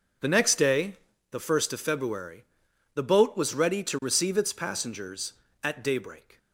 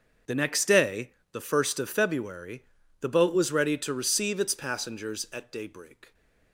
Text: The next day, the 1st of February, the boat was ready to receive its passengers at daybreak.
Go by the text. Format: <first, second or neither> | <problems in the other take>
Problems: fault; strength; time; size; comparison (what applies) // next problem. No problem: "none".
first | gets quieter; strong; throughout; 14.5 dB